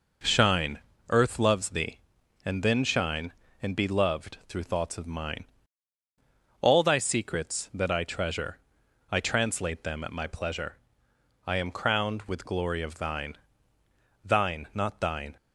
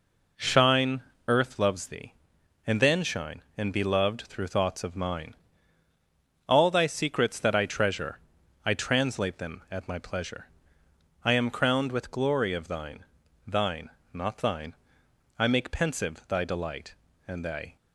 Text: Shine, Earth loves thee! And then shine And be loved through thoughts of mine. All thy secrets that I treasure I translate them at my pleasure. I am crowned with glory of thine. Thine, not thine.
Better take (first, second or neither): first